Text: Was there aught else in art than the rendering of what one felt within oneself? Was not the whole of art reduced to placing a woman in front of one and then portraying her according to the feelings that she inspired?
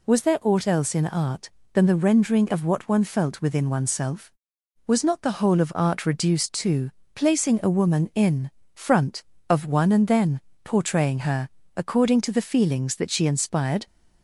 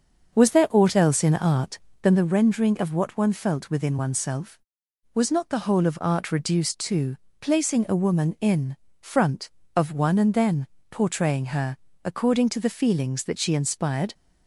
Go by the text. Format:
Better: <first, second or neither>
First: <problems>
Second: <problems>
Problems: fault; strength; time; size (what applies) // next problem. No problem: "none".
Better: first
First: pauses between "to" and "placing"; slight; at 6.8 s; 0.24 s long // pauses between "in" and "front"; slight; at 8.4 s; 0.25 s long // pauses between "then" and "portraying"; slight; at 10.4 s; 0.24 s long // pauses between "her" and "according"; slight; at 11.4 s; 0.26 s long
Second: starts louder than the rest; until 2.2 s; 6.5 dB // pauses between "to" and "placing"; slight; at 7.1 s; 0.24 s long // pauses between "in" and "front"; slight; at 8.7 s; 0.26 s long // pauses between "then" and "portraying"; slight; at 10.6 s; 0.24 s long // pauses between "her" and "according"; slight; at 11.7 s; 0.26 s long